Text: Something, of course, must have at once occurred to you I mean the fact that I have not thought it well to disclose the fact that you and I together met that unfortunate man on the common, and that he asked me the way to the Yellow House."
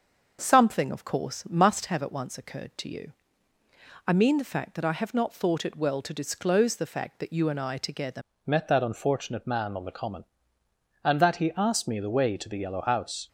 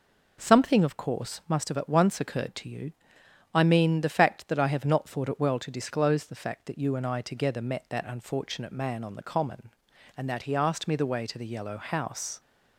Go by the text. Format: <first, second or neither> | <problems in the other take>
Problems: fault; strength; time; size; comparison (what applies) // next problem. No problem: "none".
second | starts louder than the rest; noticeable; until 1.4 s; 6 dB // pauses between "you" and "I"; noticeable; at 3.1 s; 0.96 s long; noticeable in the second // changes voice at "met"; from 8.4 s on; 4.8 s long